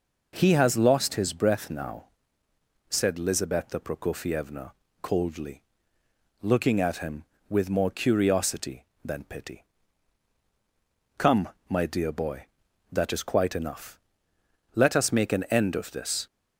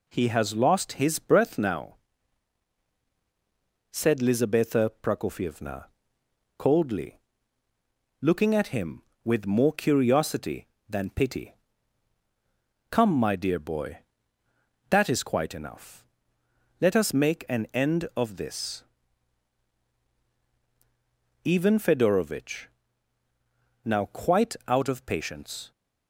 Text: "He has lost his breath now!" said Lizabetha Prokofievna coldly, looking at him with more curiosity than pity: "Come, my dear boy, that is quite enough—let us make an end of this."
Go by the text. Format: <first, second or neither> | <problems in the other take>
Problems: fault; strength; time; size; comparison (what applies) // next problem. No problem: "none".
first | pauses between "Prokofievna" and "coldly"; noticeable; at 5.8 s; 0.70 s long; slight in the first // goes on to say "Ivan Fedorovitch now quite out of patience"; strong; from 21.4 s on; 4.2 s long